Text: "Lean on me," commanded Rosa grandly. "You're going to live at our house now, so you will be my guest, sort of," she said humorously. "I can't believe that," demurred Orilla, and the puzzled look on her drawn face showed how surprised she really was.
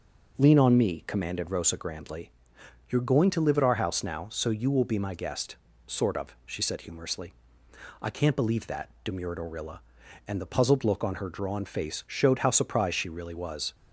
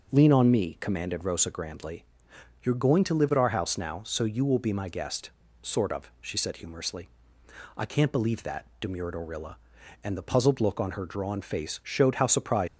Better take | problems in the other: first | stops before "she really was"; at 12.6 s

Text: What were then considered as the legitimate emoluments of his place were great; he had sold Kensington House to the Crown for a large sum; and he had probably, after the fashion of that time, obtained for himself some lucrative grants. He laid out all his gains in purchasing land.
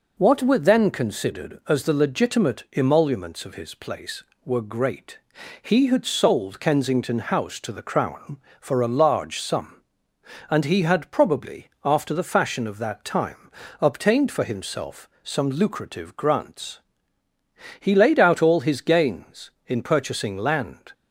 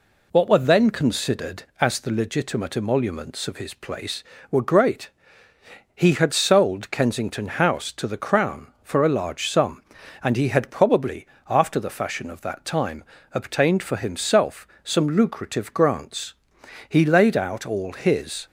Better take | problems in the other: first | pauses between "himself" and "some"; slight; at 14.6 s; 0.16 s long; slight in the first // stops before "gains in purchasing land"; at 18.4 s

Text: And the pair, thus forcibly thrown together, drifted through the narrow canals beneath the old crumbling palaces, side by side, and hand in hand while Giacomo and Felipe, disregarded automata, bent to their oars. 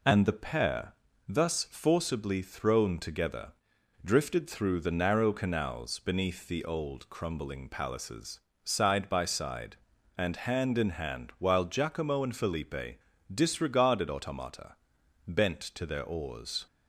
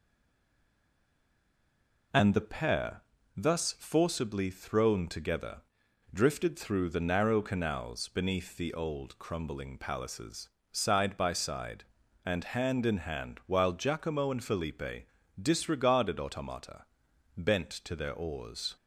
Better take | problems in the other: first | stays silent before the first word; until 2.1 s; 2.1 s long

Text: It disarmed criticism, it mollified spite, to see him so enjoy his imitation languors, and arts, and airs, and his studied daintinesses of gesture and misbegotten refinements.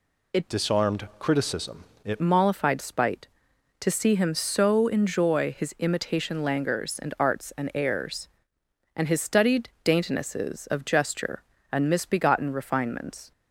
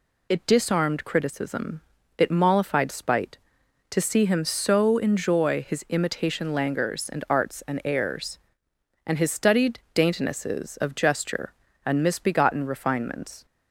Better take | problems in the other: second | changes voice from "disarmed" to "it"; from 0.4 to 2.2 s; 1.8 s long

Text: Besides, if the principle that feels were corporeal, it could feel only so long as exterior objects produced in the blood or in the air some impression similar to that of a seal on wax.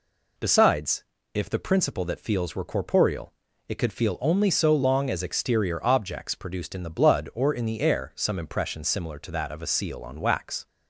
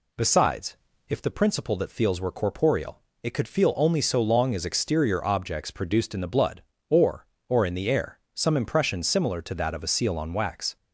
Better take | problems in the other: first | says "or" twice; at 7.4 s // pauses between "air" and "some"; slight; at 8.1 s; 0.16 s long

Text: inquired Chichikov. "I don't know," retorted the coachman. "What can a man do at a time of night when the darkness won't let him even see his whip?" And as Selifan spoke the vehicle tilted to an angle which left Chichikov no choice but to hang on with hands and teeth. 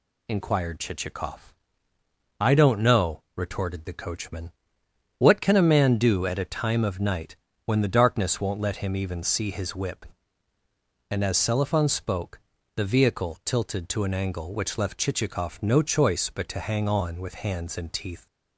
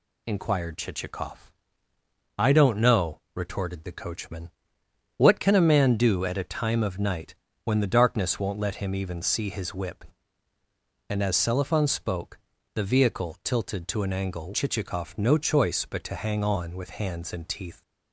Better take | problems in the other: first | pauses between "night" and "when"; slight; at 7.3 s; 0.28 s long; slight in the first // pauses between "spoke" and "the"; slight; at 12.3 s; 0.36 s long; slight in the first // skips "which left"; at 14.5 s

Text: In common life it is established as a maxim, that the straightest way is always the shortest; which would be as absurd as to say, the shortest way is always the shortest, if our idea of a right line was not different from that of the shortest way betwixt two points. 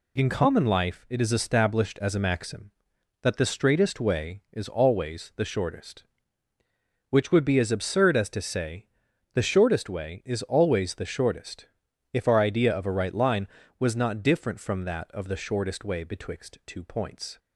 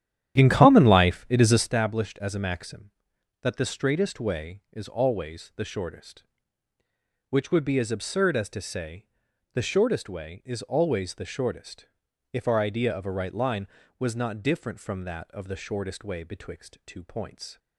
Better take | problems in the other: first | starts louder than the rest; strong; until 1.8 s; 11 dB

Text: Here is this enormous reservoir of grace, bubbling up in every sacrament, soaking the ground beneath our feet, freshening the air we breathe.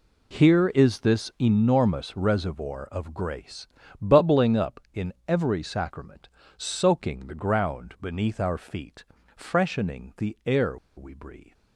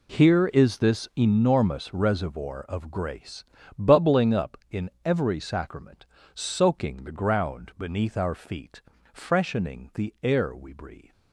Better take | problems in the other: second | pauses between "in" and "every"; slight; at 5.1 s; 0.16 s long; slight in the second // pauses between "air" and "we"; slight; at 10.7 s; 0.18 s long

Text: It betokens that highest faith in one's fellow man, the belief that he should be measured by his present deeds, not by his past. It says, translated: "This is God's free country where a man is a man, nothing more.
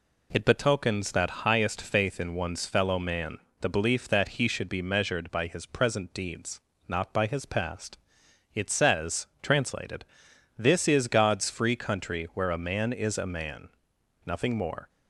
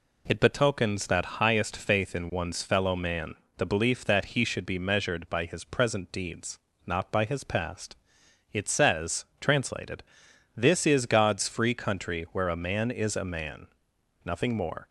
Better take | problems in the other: neither | none

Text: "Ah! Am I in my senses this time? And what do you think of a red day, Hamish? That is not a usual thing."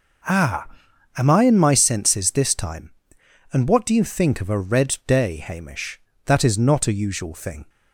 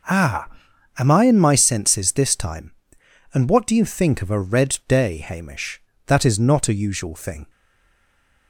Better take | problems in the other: first | stays silent after the last word; from 7.4 s on; 1.0 s long

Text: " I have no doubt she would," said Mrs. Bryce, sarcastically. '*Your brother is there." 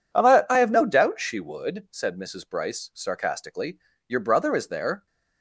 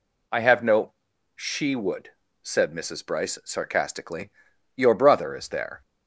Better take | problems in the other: first | skips "doubt"; at 1.1 s

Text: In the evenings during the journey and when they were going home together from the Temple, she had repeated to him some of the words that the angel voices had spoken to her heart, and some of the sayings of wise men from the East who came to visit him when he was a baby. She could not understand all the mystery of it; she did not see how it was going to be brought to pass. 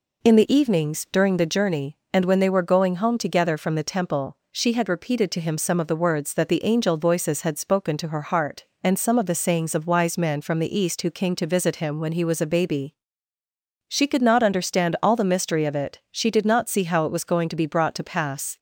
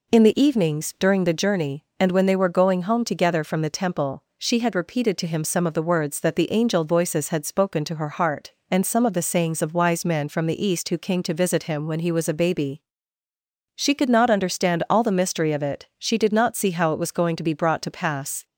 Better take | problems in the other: neither | none

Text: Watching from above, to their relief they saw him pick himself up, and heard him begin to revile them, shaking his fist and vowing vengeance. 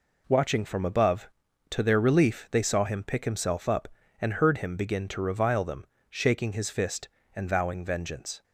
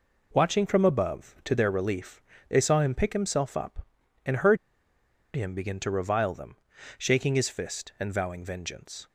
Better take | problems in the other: first | pauses between "relief" and "they"; slight; at 2.2 s; 0.26 s long // pauses between "heard" and "him"; noticeable; at 4.5 s; 0.79 s long

